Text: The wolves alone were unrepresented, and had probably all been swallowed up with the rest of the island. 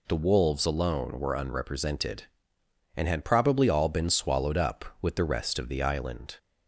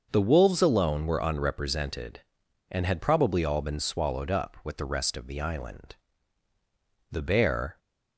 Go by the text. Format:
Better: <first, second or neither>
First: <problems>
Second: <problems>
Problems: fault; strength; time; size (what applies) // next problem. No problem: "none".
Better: first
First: none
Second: starts louder than the rest; until 1.1 s; 6 dB // goes on to say "The bear"; noticeable; from 7.1 s on; 0.68 s long